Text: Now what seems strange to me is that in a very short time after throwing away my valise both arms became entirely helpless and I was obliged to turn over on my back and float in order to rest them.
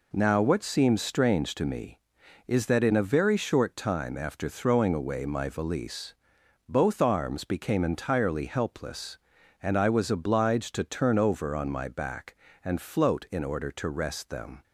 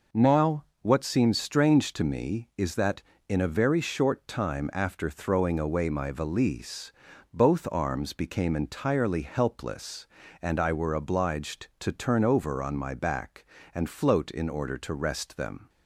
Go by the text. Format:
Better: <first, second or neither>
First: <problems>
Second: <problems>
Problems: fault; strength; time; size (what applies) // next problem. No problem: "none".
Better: first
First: pauses between "valise" and "both"; noticeable; at 6.1 s; 0.52 s long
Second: pauses between "Now" and "what"; slight; at 0.6 s; 0.18 s long // pauses between "valise" and "both"; at 6.9 s; 0.42 s long // says "were" for "was"; at 10.7 s